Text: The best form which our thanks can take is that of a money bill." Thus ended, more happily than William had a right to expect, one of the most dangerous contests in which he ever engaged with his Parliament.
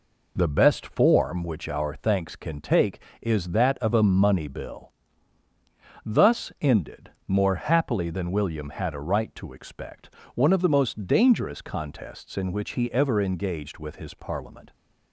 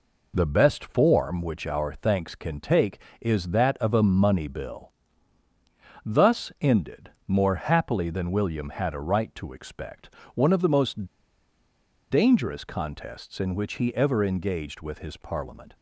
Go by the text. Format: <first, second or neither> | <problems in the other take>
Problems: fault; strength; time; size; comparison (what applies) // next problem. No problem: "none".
first | pauses between "most" and "dangerous"; at 11.0 s; 1.0 s long